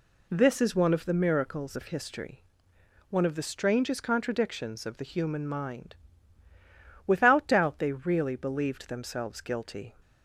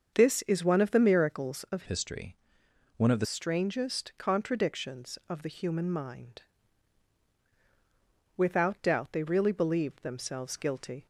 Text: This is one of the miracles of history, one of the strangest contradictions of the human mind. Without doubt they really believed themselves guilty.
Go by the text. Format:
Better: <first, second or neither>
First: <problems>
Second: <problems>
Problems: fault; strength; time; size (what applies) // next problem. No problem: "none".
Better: first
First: none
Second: starts louder than the rest; until 1.1 s; 7 dB // changes voice from "history" to "the"; from 1.8 to 3.2 s; 1.4 s long